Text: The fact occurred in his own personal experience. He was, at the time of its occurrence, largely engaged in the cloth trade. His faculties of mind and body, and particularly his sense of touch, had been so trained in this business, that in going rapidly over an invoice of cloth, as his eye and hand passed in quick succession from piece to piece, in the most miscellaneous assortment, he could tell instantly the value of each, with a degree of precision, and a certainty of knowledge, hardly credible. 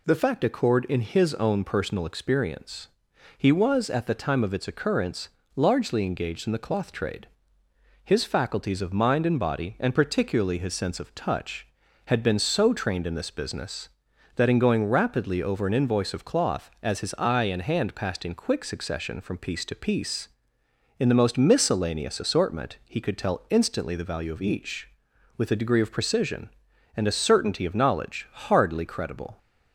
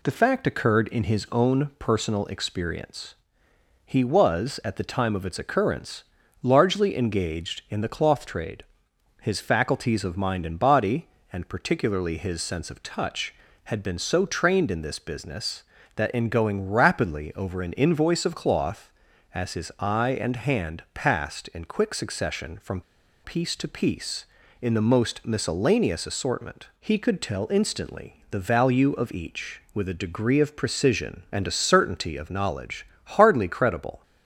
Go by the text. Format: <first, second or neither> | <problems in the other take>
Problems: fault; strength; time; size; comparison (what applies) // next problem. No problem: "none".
first | pauses between "from" and "piece"; at 22.8 s; 0.42 s long